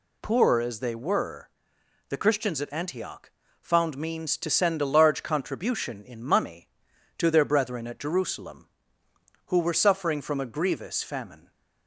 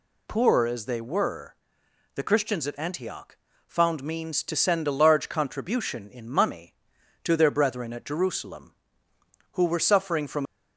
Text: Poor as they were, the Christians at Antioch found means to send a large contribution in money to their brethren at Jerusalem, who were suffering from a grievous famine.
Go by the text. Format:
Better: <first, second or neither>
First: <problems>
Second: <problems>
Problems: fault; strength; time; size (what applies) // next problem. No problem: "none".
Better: first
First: pauses between "Antioch" and "found"; slight; at 3.3 s; 0.30 s long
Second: pauses between "Antioch" and "found"; slight; at 3.3 s; 0.30 s long // stops before "a grievous famine"; at 10.4 s